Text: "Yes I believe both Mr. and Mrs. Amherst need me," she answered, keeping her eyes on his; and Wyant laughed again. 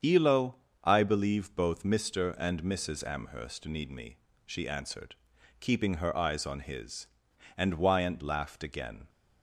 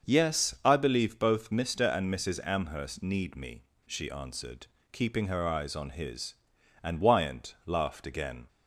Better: second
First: starts louder than the rest; strong; until 1.3 s; 7.5 dB // says "Elo" for "Yes"; at 0.0 s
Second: starts louder than the rest; until 1.1 s; 6.5 dB

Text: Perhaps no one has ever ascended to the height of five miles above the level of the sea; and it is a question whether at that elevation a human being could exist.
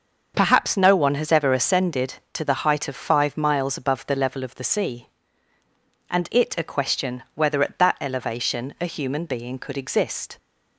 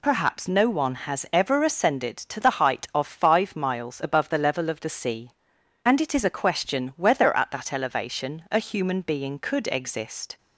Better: second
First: starts louder than the rest; until 1.3 s; 6.5 dB // skips "is"; at 6.5 s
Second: none

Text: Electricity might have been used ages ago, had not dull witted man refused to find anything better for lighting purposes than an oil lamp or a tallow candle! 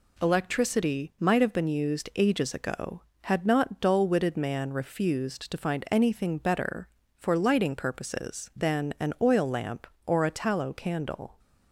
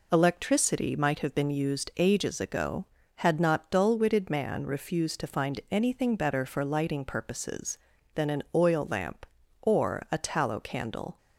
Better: neither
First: none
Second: none

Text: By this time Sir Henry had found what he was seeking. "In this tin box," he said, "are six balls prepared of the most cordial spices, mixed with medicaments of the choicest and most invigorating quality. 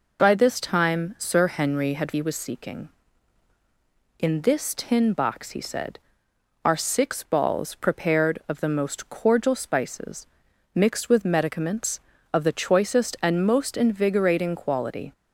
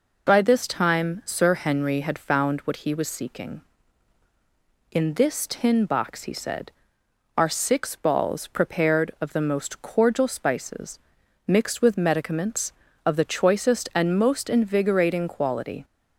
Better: second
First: skips "found what"; at 2.1 s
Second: none

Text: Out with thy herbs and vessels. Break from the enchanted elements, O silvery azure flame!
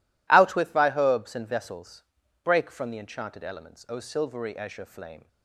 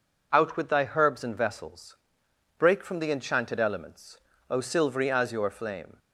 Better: neither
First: none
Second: none

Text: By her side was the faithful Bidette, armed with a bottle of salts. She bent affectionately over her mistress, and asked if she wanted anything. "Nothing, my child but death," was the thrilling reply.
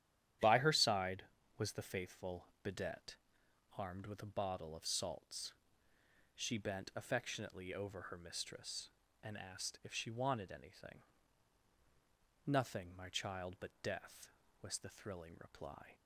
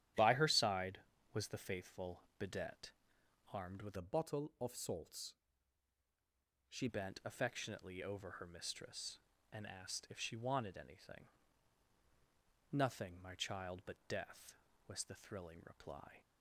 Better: first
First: starts louder than the rest; strong; until 1.7 s; 11 dB // pauses between "faithful" and "Bidette"; slight; at 2.4 s; 0.18 s long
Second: starts louder than the rest; strong; until 1.5 s; 11.5 dB // pauses between "faithful" and "Bidette"; slight; at 2.2 s; 0.18 s long // changes voice from "a" to "She"; from 3.9 to 6.8 s; 2.9 s long

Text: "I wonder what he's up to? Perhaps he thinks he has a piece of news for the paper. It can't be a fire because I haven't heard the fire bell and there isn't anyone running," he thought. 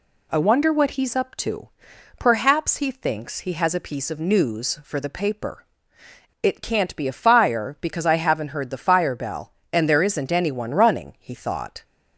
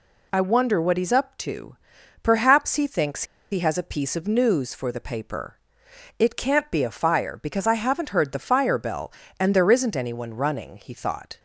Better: first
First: none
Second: pauses between "thinks" and "he"; slight; at 3.2 s; 0.27 s long

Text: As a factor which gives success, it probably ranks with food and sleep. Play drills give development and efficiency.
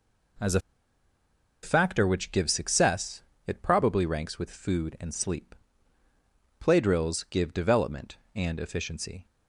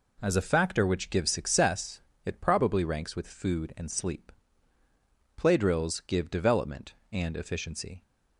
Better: second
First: pauses between "a" and "factor"; at 0.5 s; 1.0 s long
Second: none

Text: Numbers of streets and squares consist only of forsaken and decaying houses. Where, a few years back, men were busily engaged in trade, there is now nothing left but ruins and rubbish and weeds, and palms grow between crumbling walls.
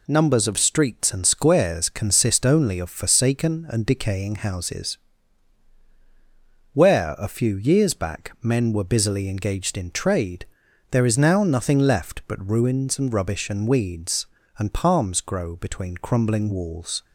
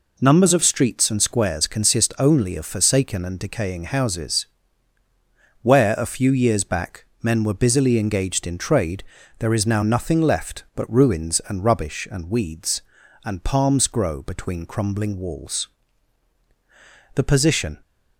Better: first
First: none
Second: goes on to say "The position"; noticeable; from 17.1 s on; 0.64 s long

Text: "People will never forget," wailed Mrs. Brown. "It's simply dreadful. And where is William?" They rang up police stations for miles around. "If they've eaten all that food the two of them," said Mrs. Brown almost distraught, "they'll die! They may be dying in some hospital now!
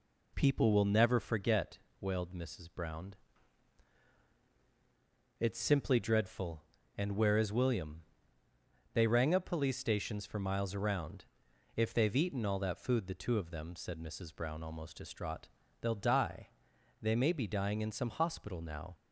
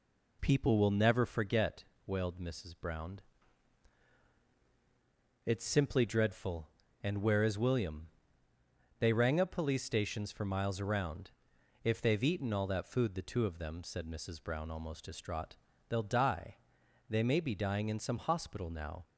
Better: neither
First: none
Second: none

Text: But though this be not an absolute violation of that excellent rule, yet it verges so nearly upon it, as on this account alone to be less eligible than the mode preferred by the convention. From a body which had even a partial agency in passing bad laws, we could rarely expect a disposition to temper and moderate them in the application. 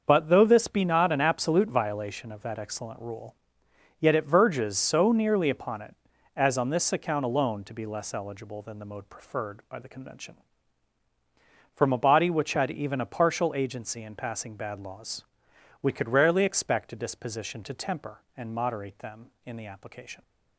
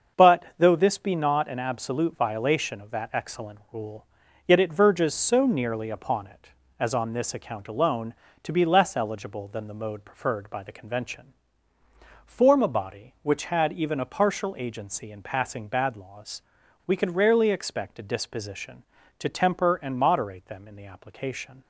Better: first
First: starts louder than the rest; until 1.0 s; 6.5 dB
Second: starts louder than the rest; until 1.3 s; 6.5 dB // says "Form" for "From"; at 12.2 s

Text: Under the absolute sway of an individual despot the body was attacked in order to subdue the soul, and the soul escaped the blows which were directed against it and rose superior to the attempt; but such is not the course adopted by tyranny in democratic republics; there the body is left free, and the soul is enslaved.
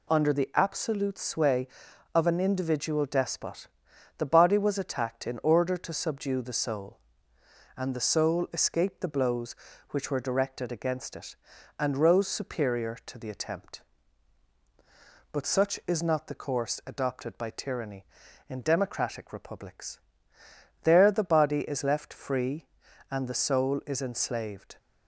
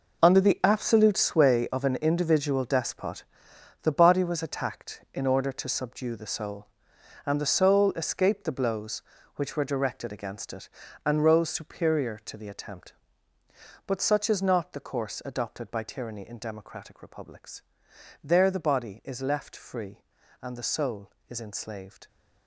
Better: first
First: pauses between "despot" and "the"; noticeable; at 3.6 s; 0.50 s long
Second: gets quieter; strong; throughout; 12 dB // pauses between "despot" and "the"; noticeable; at 3.2 s; 0.60 s long

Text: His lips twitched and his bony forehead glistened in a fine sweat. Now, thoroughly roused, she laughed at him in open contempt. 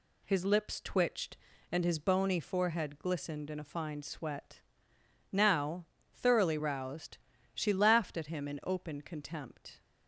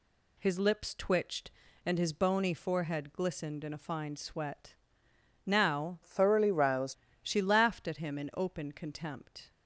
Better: first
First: none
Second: changes voice from "thoroughly" to "roused"; from 6.0 to 6.9 s; 0.9 s long

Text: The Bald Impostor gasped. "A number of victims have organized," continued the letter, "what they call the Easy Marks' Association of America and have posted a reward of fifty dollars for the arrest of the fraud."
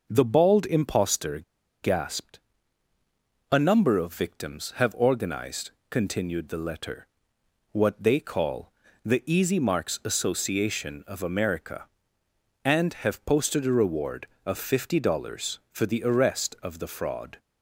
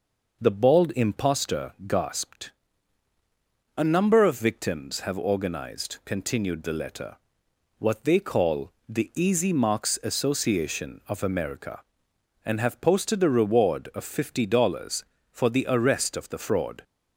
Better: second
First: pauses between "Impostor" and "gasped"; at 1.3 s; 0.44 s long // pauses between "call" and "the"; slight; at 8.7 s; 0.32 s long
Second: pauses between "call" and "the"; slight; at 8.7 s; 0.16 s long

